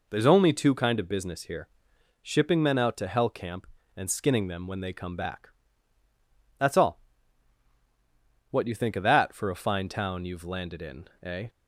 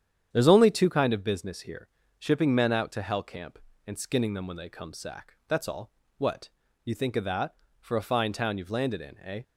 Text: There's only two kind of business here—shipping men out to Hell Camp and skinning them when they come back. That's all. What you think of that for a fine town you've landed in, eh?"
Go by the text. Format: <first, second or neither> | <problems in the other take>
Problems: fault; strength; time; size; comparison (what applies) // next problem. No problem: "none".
first | starts louder than the rest; strong; until 1.3 s; 9 dB // says "sack" for "back"; at 4.9 s // pauses between "What" and "you"; slight; at 6.5 s; 0.34 s long